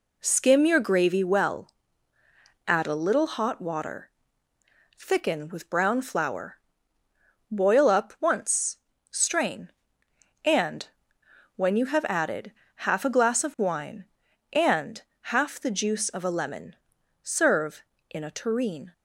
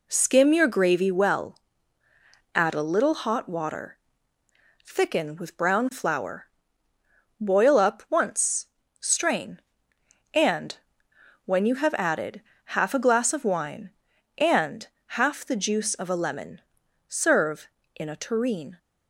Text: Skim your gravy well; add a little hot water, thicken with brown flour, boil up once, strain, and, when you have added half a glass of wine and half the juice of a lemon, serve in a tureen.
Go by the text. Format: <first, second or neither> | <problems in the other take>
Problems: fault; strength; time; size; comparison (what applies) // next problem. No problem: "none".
neither | pauses between "added" and "half"; slight; the same in both // pauses between "and" and "half"; slight; the same in both